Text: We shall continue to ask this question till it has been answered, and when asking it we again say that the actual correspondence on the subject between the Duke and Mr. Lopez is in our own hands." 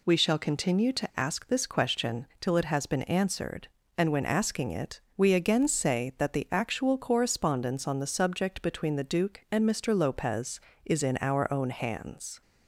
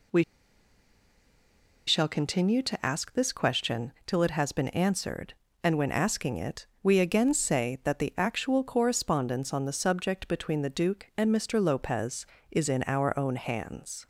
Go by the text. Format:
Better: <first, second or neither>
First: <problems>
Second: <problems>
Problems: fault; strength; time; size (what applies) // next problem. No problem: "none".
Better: first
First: pauses between "it" and "we"; slight; at 4.9 s; 0.16 s long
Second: pauses between "We" and "shall"; strong; at 0.2 s; 1.6 s long // pauses between "it" and "we"; slight; at 6.6 s; 0.16 s long